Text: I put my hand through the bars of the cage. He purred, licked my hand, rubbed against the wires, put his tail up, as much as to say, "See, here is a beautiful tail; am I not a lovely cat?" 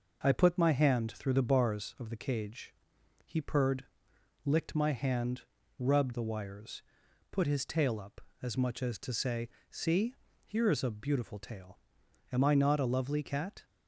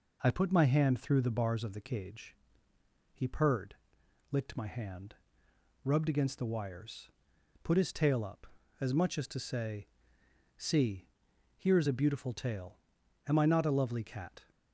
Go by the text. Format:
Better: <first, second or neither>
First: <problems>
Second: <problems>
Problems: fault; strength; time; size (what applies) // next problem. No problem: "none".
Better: second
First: skips "against"; at 6.1 s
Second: none